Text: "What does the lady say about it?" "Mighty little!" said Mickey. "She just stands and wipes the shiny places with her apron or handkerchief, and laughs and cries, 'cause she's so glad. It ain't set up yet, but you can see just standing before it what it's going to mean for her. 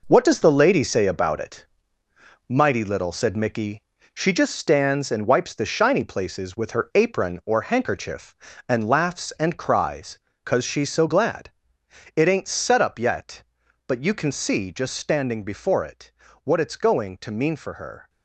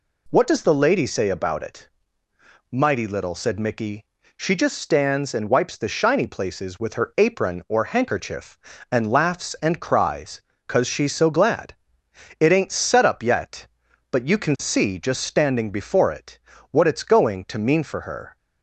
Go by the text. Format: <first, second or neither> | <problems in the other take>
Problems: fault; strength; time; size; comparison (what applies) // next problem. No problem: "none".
second | gets quieter; strong; throughout; 7.5 dB // pauses between "it" and "what"; slight; at 16.1 s; 0.32 s long; slight in the second